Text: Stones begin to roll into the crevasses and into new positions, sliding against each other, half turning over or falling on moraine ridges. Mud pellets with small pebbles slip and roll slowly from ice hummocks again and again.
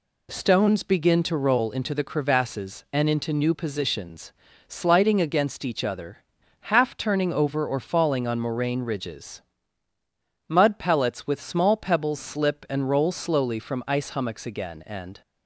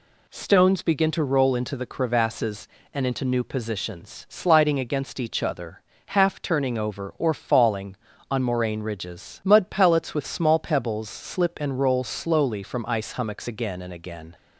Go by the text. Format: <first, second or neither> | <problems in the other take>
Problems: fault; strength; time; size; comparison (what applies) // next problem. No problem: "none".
second | stops before "again"; at 15.2 s